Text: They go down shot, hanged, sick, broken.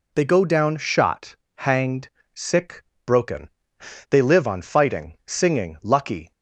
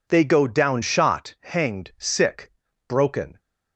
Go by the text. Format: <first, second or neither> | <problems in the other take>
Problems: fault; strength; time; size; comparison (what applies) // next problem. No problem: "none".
second | goes on to say "They live on fighting singing lucky"; strong; from 4.1 s on; 2.2 s long